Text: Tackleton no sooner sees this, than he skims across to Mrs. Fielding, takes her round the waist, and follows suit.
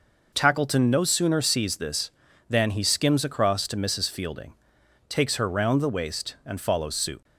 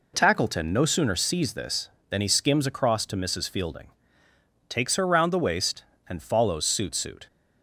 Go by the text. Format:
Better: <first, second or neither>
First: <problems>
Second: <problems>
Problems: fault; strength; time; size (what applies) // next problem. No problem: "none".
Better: first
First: none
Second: says "suit" twice; at 6.9 s